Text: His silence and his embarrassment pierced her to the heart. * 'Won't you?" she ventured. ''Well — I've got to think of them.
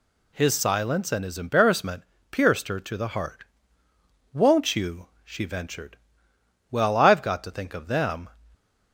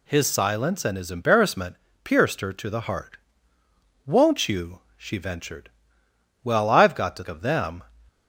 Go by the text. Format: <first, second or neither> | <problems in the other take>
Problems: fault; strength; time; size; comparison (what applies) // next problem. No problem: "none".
first | pauses between "embarrassment" and "pierced"; slight; at 1.7 s; 0.26 s long; slight in the first // skips "think"; at 7.2 s